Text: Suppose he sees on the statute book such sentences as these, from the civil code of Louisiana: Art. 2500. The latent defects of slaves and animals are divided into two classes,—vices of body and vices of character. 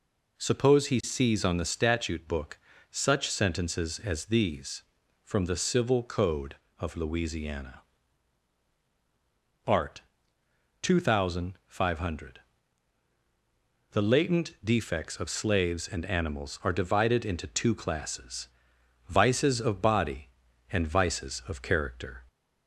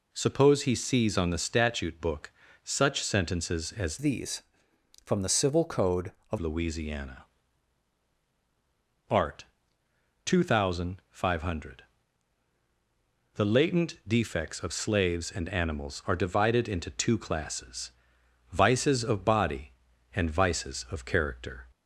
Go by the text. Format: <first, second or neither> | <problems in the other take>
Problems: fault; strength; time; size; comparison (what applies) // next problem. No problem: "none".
first | pauses between "book" and "such"; slight; at 2.3 s; 0.32 s long; slight in the first // changes voice from "these" to "of"; from 3.9 to 6.3 s; 2.4 s long